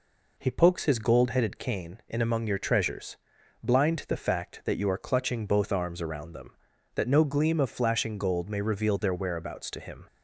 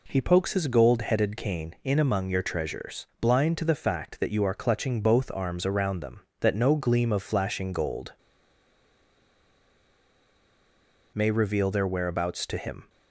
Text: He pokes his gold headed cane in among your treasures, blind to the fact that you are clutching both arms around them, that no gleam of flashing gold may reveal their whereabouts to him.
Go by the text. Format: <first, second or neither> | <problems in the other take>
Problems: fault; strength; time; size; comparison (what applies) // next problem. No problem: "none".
first | pauses between "gold" and "may"; strong; at 8.1 s; 3.0 s long